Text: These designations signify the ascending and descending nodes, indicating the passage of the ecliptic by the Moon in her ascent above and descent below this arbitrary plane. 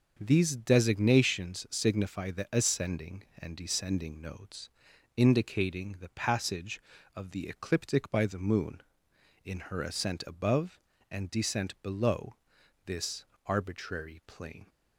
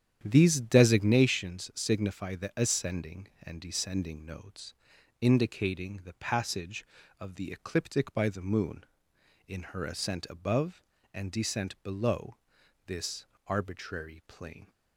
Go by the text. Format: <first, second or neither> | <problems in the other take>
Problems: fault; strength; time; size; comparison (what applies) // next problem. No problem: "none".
first | starts louder than the rest; strong; until 1.2 s; 9.5 dB // pauses between "below" and "this"; noticeable; at 12.3 s; 0.50 s long; noticeable in the first // pauses between "this" and "arbitrary"; slight; at 13.2 s; 0.22 s long; slight in the first